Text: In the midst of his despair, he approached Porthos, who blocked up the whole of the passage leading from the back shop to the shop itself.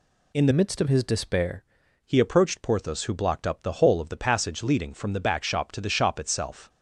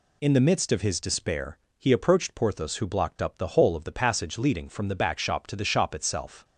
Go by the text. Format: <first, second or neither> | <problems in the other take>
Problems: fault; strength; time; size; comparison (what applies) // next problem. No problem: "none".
second | changes voice from "midst" to "despair"; from 0.5 to 1.6 s; 1.1 s long